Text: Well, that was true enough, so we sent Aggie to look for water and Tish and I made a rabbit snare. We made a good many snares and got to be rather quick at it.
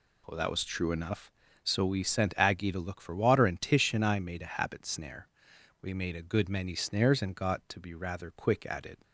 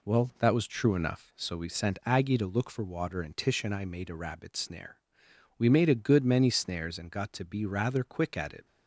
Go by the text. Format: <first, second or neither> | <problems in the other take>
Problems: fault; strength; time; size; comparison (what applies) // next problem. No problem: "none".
second | says "habit" for "rabbit"; at 4.5 s